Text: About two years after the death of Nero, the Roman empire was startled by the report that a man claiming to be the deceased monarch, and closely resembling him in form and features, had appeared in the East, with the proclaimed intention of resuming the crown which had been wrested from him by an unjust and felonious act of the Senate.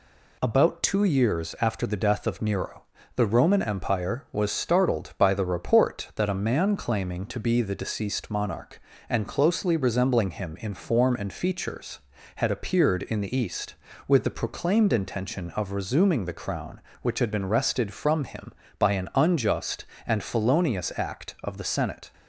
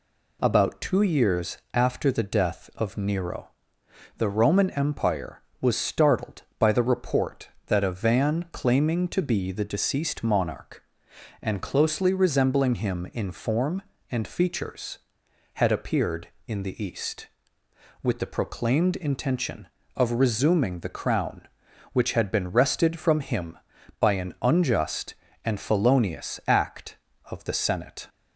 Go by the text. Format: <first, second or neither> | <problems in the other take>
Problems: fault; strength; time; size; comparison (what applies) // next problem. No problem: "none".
first | pauses between "years" and "after"; slight; at 1.5 s; 0.16 s long // says "van" for "man"; at 7.9 s